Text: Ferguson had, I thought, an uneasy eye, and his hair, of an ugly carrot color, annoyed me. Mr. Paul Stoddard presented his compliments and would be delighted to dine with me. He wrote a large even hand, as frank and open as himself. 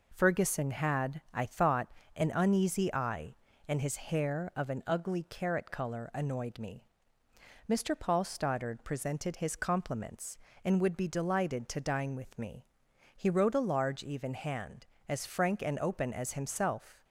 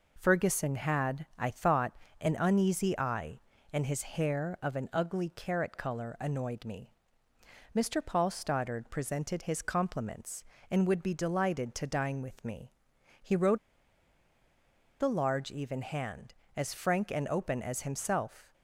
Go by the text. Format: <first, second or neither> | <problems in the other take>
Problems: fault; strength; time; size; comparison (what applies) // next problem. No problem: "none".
first | pauses between "wrote" and "a"; strong; at 13.5 s; 1.4 s long